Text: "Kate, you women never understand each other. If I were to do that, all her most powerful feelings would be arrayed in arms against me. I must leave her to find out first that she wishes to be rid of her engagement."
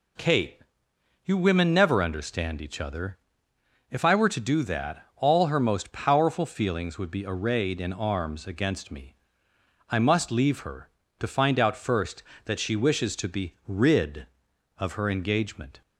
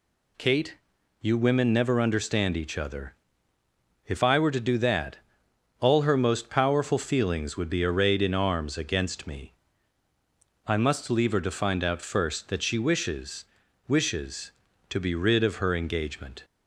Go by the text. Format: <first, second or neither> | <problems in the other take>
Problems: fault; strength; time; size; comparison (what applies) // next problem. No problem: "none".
first | says "wishes" twice; at 13.8 s